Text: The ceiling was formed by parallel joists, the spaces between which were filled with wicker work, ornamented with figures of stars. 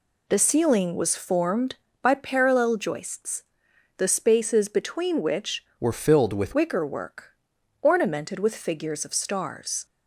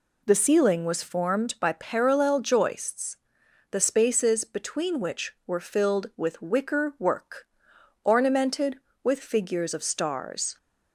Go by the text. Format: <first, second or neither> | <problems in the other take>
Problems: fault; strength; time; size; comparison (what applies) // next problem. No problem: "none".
second | changes voice from "were" to "with"; from 5.7 to 6.5 s; 0.8 s long